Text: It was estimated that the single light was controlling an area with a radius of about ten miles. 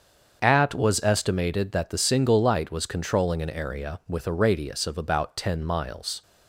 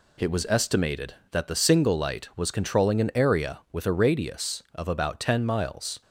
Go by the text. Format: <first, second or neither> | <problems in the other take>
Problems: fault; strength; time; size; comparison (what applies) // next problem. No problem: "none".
second | starts louder than the rest; until 1.4 s; 7 dB // says "At" for "It"; at 0.4 s